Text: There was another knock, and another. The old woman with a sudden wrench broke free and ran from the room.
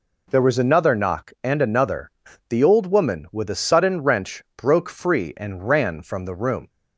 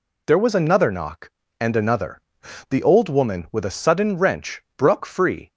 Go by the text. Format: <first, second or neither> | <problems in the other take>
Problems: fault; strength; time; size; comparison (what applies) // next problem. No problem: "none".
first | pauses between "wrench" and "broke"; slight; at 4.6 s; 0.16 s long // stops before "and ran from the room"; at 5.5 s